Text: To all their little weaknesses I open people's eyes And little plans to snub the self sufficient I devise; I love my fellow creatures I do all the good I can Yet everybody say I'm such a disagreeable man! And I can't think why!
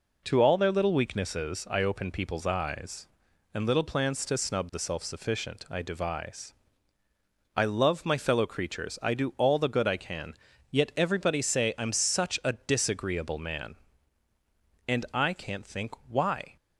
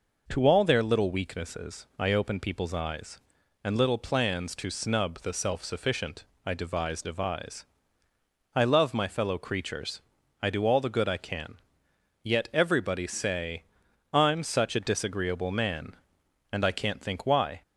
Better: first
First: pauses between "can" and "Yet"; slight; at 10.3 s; 0.36 s long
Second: pauses between "sufficient" and "I"; slight; at 6.2 s; 0.20 s long // says "devise" twice; at 7.0 s // pauses between "creatures" and "I"; at 10.0 s; 0.40 s long // pauses between "can" and "Yet"; noticeable; at 11.5 s; 0.66 s long // pauses between "say" and "I'm"; noticeable; at 13.6 s; 0.50 s long

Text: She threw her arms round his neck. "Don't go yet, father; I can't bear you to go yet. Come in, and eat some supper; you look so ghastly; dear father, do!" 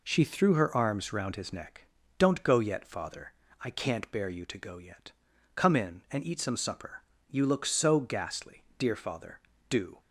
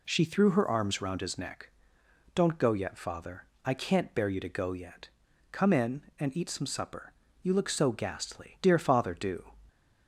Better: neither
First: none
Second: none

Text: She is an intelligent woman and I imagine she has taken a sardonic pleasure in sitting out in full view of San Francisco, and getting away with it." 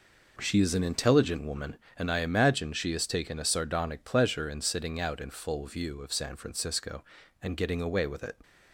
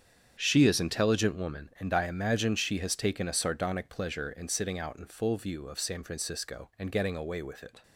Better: first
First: none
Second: starts louder than the rest; strong; until 1.4 s; 8.5 dB // skips "an"; at 0.7 s

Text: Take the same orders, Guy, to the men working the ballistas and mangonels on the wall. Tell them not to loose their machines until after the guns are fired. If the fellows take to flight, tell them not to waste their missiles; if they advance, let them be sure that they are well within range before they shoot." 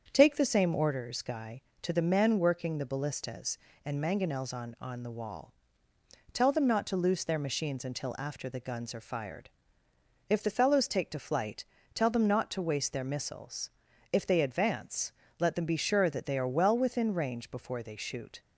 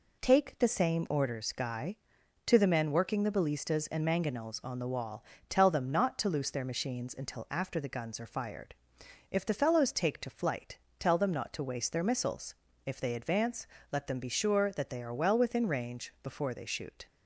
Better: second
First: starts louder than the rest; strong; until 1.1 s; 7.5 dB // says "on" twice; at 4.8 s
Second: none

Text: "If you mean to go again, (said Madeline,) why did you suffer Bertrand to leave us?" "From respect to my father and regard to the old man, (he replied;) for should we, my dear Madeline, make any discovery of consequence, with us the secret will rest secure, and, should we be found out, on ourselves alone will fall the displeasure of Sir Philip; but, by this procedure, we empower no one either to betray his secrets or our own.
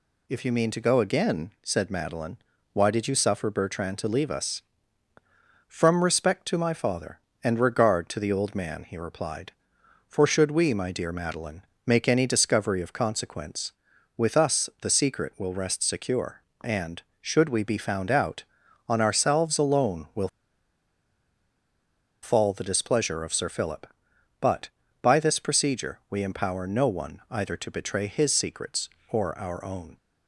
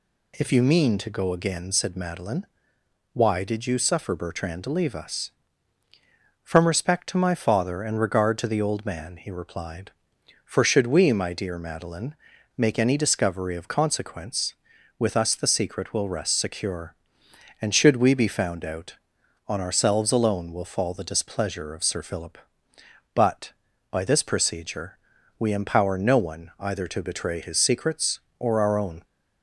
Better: second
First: pauses between "will" and "fall"; strong; at 20.2 s; 1.9 s long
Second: none

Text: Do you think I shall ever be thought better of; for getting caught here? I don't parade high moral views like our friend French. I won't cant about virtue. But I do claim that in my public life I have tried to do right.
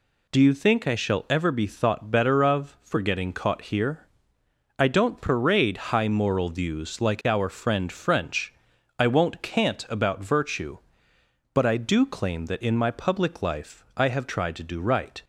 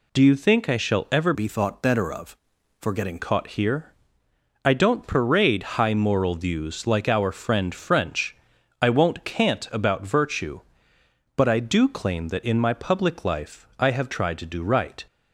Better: first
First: pauses between "parade" and "high"; slight; at 5.7 s; 0.18 s long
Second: changes voice from "be" to "getting"; from 1.3 to 3.1 s; 1.8 s long // pauses between "parade" and "high"; slight; at 5.6 s; 0.18 s long

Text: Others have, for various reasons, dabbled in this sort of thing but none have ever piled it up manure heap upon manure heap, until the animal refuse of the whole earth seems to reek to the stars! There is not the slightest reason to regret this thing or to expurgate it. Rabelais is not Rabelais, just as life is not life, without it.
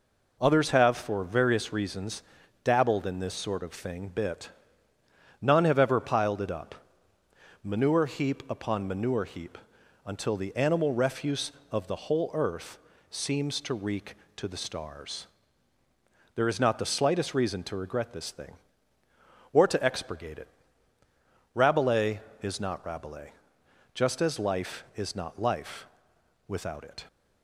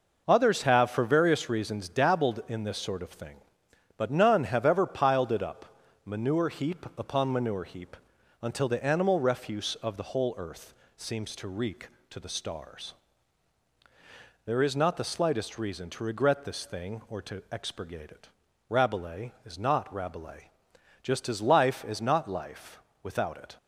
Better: second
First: says "bit" for "but"; at 4.0 s // pauses between "up" and "manure"; noticeable; at 6.7 s; 0.88 s long // pauses between "earth" and "seems"; slight; at 12.7 s; 0.34 s long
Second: pauses between "up" and "manure"; slight; at 5.7 s; 0.28 s long // pauses between "earth" and "seems"; slight; at 10.7 s; 0.24 s long

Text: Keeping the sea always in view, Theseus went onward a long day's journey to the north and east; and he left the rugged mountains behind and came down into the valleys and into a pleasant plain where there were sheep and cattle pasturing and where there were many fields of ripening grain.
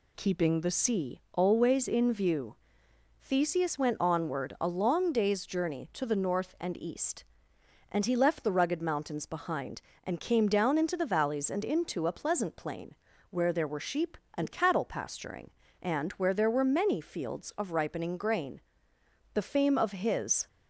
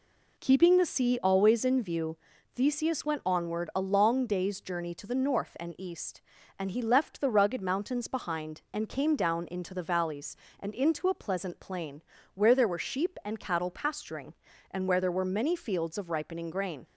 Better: second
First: pauses between "plain" and "where"; slight; at 12.9 s; 0.34 s long // goes on to say "The fame of his"; noticeable; from 19.3 s on; 1.1 s long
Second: pauses between "plain" and "where"; slight; at 12.0 s; 0.32 s long

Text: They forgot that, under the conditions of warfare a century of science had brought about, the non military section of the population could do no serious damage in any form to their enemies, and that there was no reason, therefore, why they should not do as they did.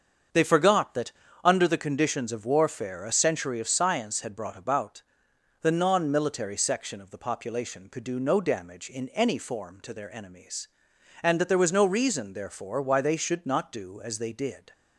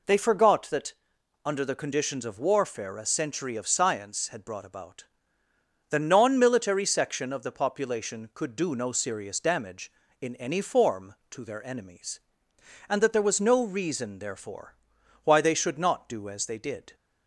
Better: second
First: starts louder than the rest; strong; until 1.6 s; 7.5 dB // skips "serious"; at 8.4 s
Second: none

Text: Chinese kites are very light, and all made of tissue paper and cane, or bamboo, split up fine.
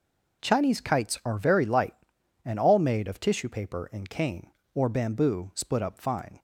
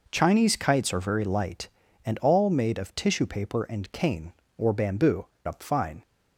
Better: first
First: none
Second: skips "split"; at 5.3 s

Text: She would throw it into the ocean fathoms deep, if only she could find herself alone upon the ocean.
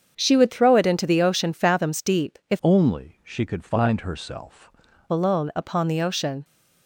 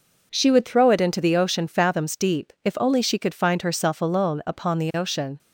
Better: second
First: starts louder than the rest; strong; until 1.1 s; 7.5 dB // changes voice from "only" to "herself"; from 2.6 to 4.7 s; 2.1 s long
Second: none

